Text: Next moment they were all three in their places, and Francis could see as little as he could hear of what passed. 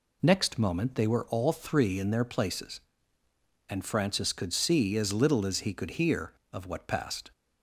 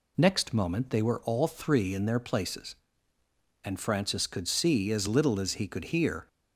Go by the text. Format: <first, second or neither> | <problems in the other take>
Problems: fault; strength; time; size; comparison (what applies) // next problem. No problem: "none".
first | stops before "of what passed"; at 6.2 s